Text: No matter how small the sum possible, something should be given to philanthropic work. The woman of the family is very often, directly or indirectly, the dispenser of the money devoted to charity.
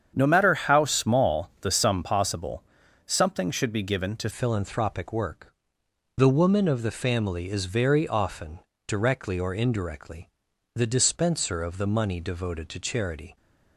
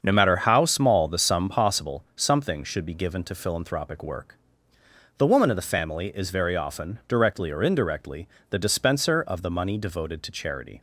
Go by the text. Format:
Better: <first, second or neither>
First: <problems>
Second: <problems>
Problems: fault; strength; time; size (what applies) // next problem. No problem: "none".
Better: second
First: starts louder than the rest; strong; until 1.1 s; 8 dB // changes voice at "philanthropic"; from 4.3 s on; 9.0 s long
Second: starts louder than the rest; until 1.0 s; 7 dB